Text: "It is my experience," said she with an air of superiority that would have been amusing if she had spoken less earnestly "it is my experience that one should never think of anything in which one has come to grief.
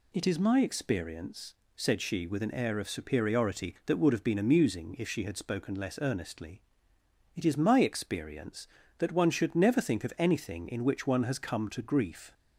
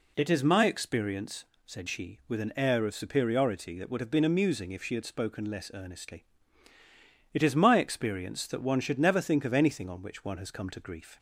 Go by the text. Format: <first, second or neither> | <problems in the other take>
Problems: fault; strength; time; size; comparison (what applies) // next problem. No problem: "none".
first | pauses between "earnestly" and "it"; at 6.2 s; 1.0 s long; noticeable in the first // says "on" for "in"; at 9.8 s